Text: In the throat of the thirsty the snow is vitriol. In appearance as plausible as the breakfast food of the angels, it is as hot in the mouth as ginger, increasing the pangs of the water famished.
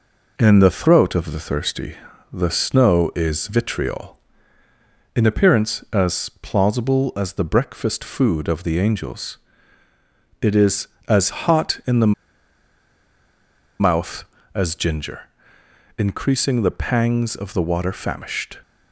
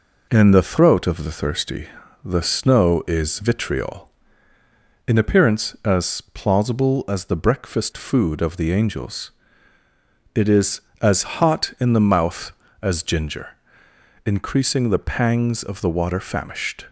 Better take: second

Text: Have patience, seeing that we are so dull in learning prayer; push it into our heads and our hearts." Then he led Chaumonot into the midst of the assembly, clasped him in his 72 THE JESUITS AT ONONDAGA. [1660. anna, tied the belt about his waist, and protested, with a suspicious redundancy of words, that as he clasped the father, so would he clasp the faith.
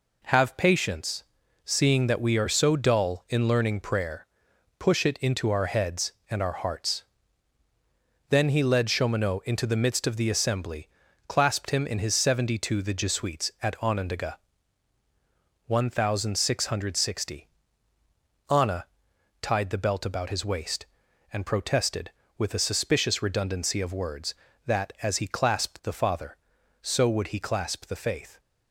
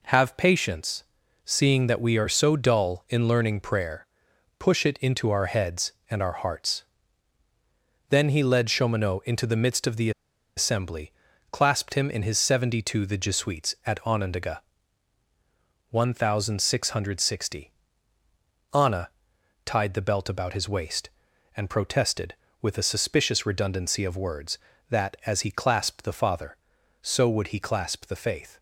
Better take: first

